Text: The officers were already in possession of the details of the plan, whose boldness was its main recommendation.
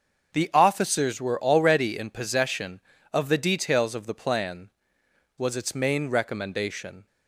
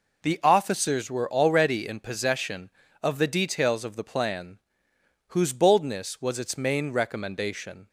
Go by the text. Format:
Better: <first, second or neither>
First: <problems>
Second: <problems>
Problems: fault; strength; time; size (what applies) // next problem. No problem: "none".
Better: second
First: starts louder than the rest; until 1.3 s; 6.5 dB // skips "whose boldness"; at 5.0 s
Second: none